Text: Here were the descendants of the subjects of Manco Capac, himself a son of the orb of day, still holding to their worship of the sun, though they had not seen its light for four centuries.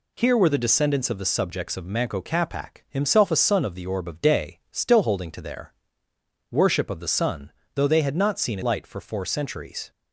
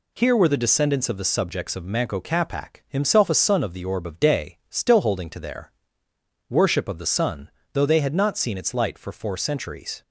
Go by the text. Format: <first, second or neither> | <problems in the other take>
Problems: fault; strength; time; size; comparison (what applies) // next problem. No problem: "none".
second | pauses between "their" and "worship"; noticeable; at 5.7 s; 0.78 s long; noticeable in the second // skips "its"; at 8.6 s